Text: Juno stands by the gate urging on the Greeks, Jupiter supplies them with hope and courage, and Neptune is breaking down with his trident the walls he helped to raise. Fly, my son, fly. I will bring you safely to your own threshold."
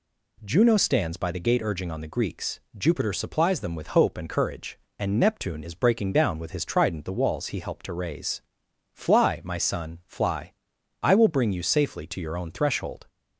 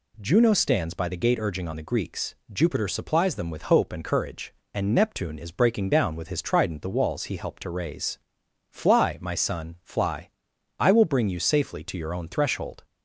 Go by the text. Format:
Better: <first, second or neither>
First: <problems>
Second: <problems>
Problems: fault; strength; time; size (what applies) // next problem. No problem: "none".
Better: neither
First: none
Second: none